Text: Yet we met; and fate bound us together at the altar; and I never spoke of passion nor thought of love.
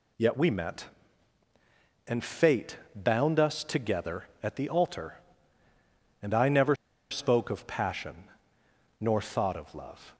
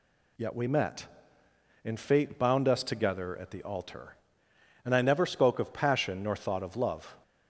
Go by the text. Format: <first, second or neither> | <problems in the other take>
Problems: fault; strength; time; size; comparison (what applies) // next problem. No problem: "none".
second | pauses between "fate" and "bound"; slight; at 2.7 s; 0.18 s long // pauses between "never" and "spoke"; slight; at 6.7 s; 0.34 s long // pauses between "passion" and "nor"; noticeable; at 8.2 s; 0.74 s long